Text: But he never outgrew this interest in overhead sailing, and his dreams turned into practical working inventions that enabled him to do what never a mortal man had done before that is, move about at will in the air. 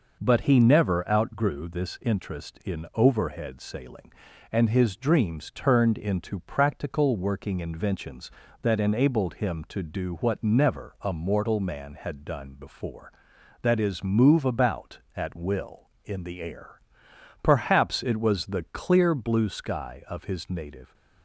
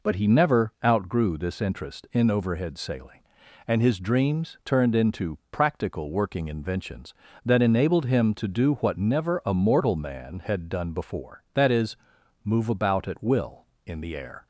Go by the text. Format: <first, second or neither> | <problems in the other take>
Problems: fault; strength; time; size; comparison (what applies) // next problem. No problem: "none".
second | goes on to say "Perhaps it was the clear blue sky of his native"; strong; from 17.4 s on; 3.5 s long